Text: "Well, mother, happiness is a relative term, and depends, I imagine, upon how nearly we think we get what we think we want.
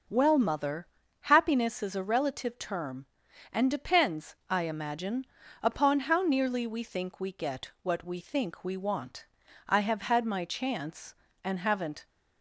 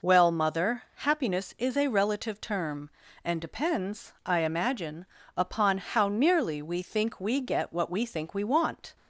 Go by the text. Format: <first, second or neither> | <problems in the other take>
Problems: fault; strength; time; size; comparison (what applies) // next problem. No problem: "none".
second | goes on to say "I have had my chance and haven't"; strong; from 9.6 s on; 2.3 s long